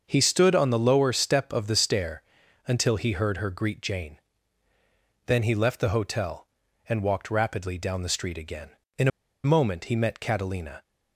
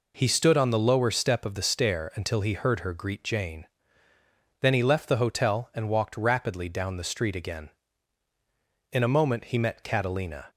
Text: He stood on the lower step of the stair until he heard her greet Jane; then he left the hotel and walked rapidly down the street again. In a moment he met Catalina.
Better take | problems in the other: second | starts louder than the rest; until 1.0 s; 6.5 dB // pauses between "stair" and "until"; at 2.2 s; 0.44 s long // pauses between "In" and "a"; slight; at 9.0 s; 0.35 s long

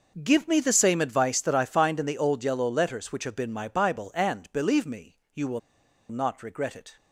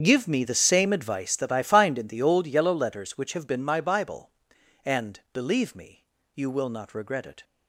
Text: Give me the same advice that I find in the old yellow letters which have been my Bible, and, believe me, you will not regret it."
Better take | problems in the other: second | starts louder than the rest; until 1.2 s; 6 dB; strong in the second // pauses between "will" and "not"; noticeable; at 5.5 s; 0.51 s long

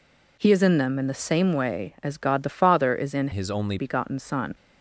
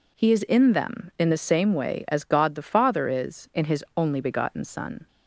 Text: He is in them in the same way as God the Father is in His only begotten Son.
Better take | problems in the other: second | changes voice from "His" to "only"; from 3.3 to 3.7 s; 0.4 s long

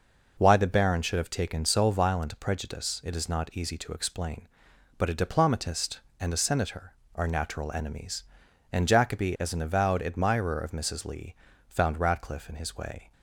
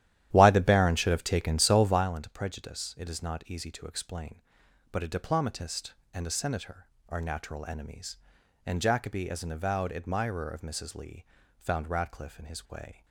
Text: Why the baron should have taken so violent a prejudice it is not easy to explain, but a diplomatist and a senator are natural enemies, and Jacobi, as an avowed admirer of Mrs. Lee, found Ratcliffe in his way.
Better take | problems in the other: first | starts louder than the rest; strong; until 2.2 s; 12 dB

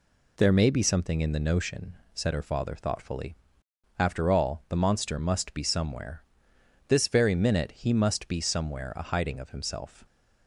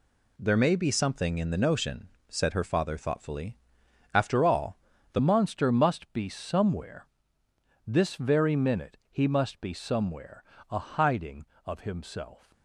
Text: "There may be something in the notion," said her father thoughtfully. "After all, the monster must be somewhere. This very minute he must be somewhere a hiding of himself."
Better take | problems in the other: first | changes voice at "monster"; from 5.1 s on; 7.4 s long // pauses between "somewhere" and "a"; slight; at 10.4 s; 0.28 s long

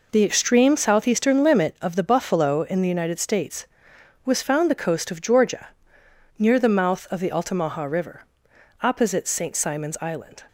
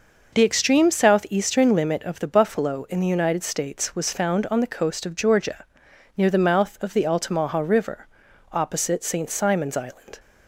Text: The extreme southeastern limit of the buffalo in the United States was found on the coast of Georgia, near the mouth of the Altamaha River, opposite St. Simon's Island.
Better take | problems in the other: second | skips "on"; at 4.7 s

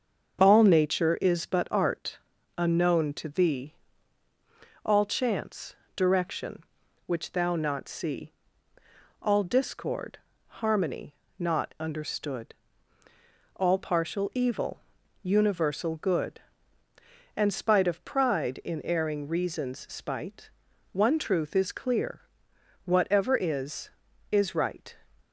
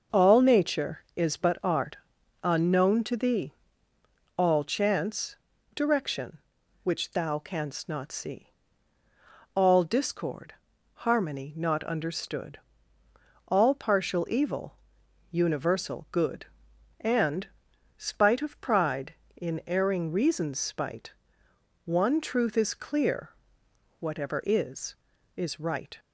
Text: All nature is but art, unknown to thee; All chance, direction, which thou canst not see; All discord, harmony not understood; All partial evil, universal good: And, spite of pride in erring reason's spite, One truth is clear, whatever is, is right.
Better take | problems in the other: second | starts louder than the rest; until 1.4 s; 7 dB // skips "canst"; at 7.5 s // pauses between "harmony" and "not"; slight; at 11.1 s; 0.24 s long

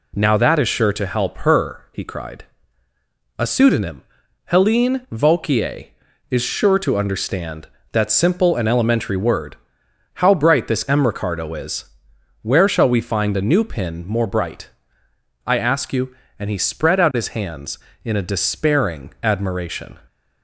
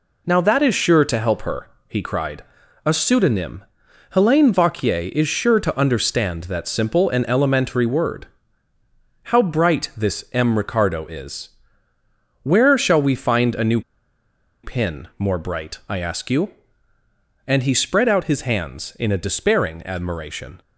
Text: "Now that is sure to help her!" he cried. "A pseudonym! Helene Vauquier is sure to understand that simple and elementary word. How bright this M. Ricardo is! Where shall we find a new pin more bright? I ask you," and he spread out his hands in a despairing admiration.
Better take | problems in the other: first | pauses between "new" and "pin"; noticeable; at 13.8 s; 0.83 s long

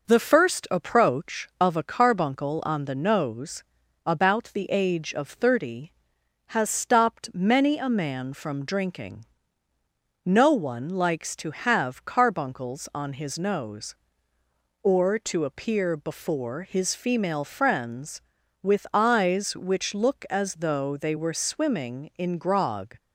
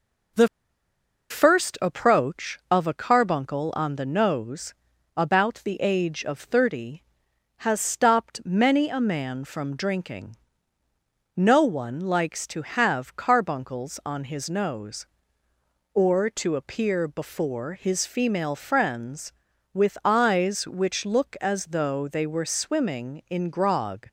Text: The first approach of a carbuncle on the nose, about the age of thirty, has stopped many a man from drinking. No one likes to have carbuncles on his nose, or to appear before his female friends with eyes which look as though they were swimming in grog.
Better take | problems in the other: first | pauses between "The" and "first"; noticeable; at 0.4 s; 0.82 s long

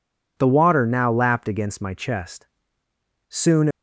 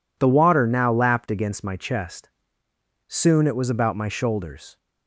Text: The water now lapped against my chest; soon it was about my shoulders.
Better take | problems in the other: second | stops before "it was about my shoulders"; at 3.7 s

